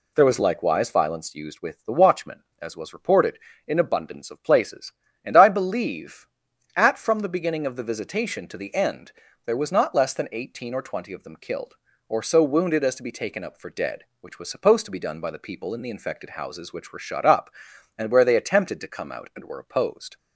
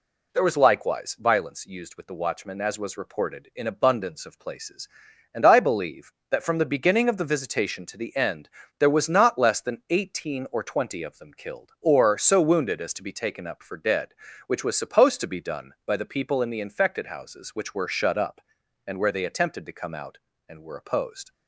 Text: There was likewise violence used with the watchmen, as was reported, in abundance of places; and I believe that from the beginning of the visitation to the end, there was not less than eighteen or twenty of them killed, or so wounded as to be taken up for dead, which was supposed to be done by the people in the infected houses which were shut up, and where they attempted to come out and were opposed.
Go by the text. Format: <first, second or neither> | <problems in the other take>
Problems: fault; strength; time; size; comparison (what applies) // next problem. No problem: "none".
second | says "at" for "that"; at 6.7 s